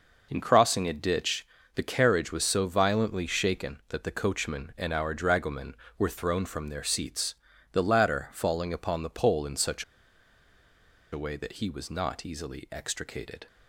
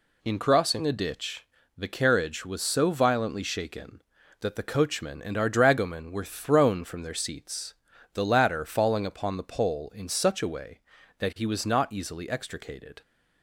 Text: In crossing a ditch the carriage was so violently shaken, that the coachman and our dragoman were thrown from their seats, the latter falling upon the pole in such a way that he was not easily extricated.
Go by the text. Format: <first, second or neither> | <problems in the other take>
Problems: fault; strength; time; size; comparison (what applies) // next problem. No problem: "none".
second | pauses between "ditch" and "the"; slight; at 1.4 s; 0.28 s long; slight in the second // pauses between "such" and "a"; strong; at 9.8 s; 1.2 s long